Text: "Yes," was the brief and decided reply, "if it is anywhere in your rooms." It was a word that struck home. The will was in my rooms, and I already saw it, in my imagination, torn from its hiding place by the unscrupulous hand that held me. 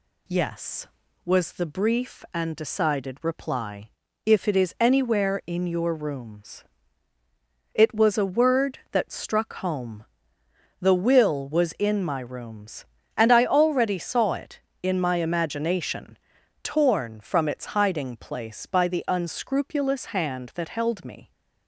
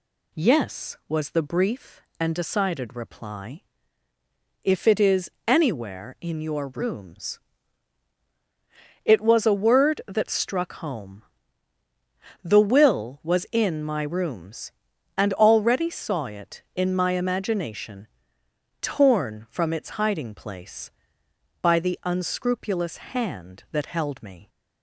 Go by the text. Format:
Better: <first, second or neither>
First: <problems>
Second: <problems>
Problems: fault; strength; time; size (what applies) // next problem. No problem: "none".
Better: first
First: none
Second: pauses between "is" and "anywhere"; slight; at 5.3 s; 0.16 s long // skips "I"; at 15.3 s